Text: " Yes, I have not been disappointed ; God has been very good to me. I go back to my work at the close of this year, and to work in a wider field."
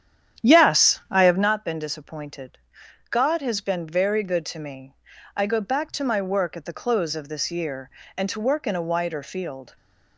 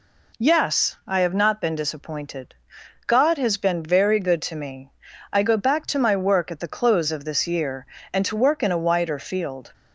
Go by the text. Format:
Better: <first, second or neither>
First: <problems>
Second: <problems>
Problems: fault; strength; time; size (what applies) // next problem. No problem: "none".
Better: second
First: starts louder than the rest; strong; until 1.5 s; 9.5 dB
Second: none